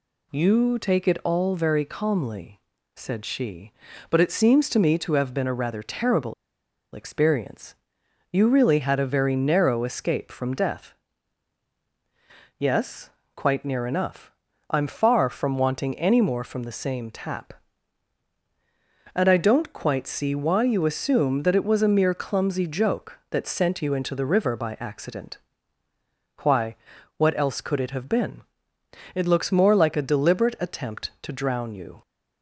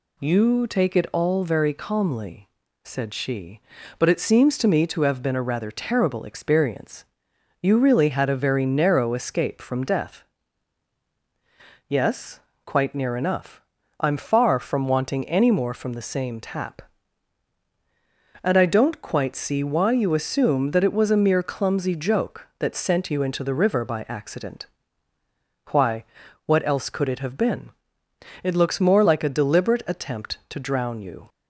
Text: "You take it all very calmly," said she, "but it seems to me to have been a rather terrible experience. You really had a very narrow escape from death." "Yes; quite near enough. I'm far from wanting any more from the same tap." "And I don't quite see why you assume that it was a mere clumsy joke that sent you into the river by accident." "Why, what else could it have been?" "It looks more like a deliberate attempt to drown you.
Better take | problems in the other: second | pauses between "terrible" and "experience"; noticeable; at 6.3 s; 0.59 s long

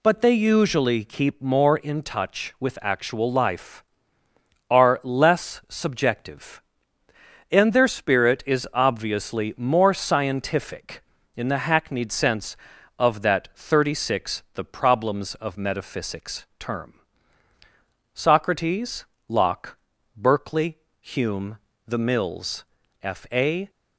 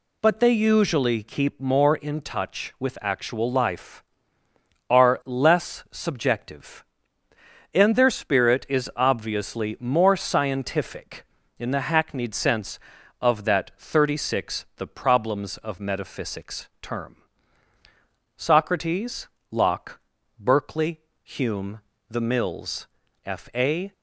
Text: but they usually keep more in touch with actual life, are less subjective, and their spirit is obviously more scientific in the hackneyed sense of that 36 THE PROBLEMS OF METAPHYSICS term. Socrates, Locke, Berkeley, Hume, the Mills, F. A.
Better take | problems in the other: neither | pauses between "METAPHYSICS" and "term"; slight; the same in both

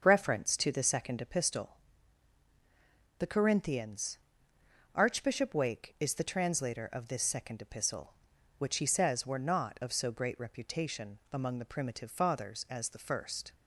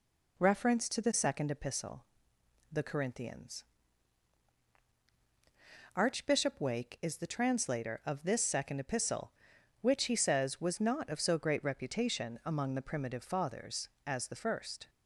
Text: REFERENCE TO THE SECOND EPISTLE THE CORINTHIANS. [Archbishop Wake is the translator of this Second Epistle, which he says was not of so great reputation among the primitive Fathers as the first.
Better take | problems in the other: second | starts louder than the rest; until 1.0 s; 6.5 dB // pauses between "EPISTLE" and "THE"; strong; at 1.7 s; 1.4 s long; noticeable in the second // says "were" for "was"; at 9.2 s

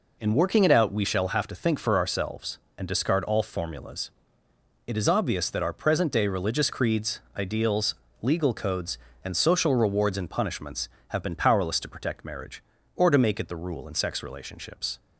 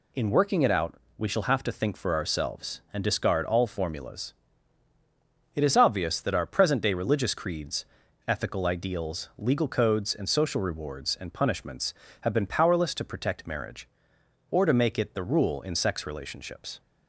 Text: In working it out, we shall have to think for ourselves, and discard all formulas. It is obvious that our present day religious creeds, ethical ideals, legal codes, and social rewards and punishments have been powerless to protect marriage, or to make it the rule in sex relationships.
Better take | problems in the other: second | skips "ethical"; at 7.2 s

